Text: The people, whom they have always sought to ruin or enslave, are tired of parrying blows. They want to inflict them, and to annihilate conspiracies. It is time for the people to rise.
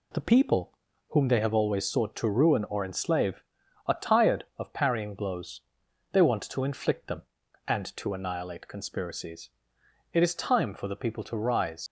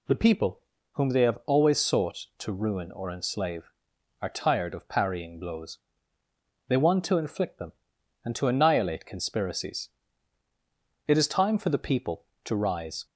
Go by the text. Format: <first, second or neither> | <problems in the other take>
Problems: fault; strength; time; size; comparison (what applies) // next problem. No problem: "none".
second | leaves "rise" unfinished; at 11.8 s; 80 ms